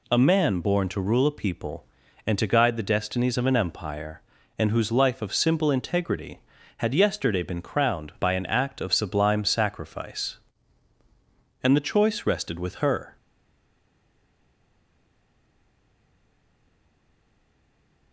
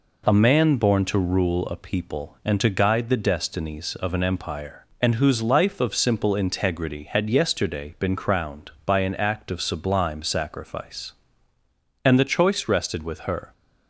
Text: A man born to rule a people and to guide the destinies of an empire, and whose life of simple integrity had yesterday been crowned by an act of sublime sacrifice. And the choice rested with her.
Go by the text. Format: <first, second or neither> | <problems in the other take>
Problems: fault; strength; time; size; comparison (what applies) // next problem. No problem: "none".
second | stays silent after the last word; strong; from 13.1 s on; 5.0 s long